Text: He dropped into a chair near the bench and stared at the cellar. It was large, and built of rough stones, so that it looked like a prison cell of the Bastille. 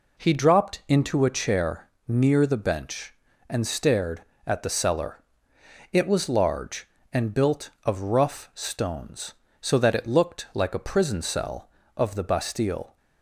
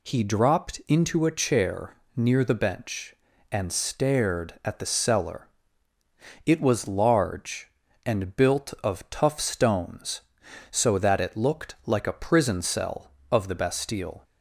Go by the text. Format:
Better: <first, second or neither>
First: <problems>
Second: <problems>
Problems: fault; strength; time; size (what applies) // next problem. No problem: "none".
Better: first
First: pauses between "chair" and "near"; slight; at 1.8 s; 0.20 s long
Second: pauses between "chair" and "near"; slight; at 1.9 s; 0.20 s long // says "tough" for "rough"; at 9.0 s